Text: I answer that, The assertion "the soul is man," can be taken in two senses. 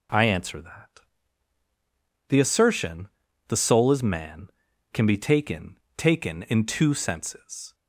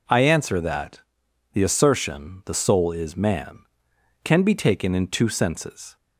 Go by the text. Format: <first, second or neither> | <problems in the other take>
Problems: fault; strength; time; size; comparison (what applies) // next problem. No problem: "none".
second | pauses between "assertion" and "the"; at 3.0 s; 0.40 s long // says "taken" twice; at 5.9 s